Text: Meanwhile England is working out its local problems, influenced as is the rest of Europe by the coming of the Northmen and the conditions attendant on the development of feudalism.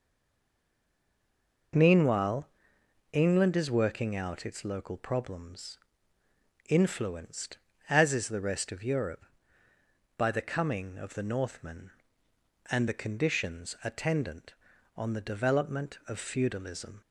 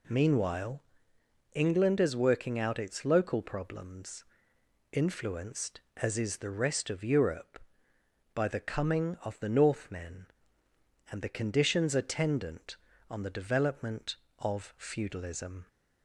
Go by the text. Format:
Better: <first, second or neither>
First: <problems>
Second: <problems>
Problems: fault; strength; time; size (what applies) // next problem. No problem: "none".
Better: second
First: stays silent before the first word; noticeable; until 1.7 s; 1.7 s long // pauses between "Meanwhile" and "England"; noticeable; at 2.4 s; 0.62 s long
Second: pauses between "Meanwhile" and "England"; noticeable; at 0.8 s; 0.72 s long